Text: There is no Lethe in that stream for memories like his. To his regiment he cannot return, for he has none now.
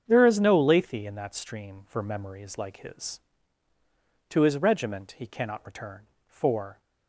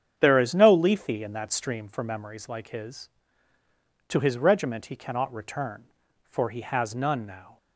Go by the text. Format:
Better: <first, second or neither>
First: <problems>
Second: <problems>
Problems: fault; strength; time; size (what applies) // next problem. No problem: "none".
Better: second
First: starts louder than the rest; strong; until 1.0 s; 7.5 dB // stops before "he has none now"; at 6.7 s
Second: starts louder than the rest; strong; until 1.1 s; 8 dB